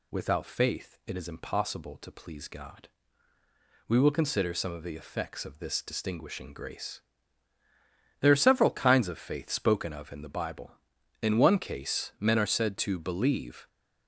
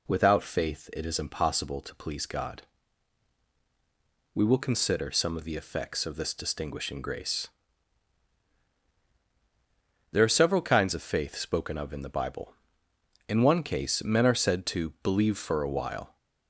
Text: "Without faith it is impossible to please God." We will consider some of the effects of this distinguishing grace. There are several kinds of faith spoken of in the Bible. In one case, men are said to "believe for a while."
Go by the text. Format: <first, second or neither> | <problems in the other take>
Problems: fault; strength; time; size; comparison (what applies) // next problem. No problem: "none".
second | stops before "for a while"; at 13.6 s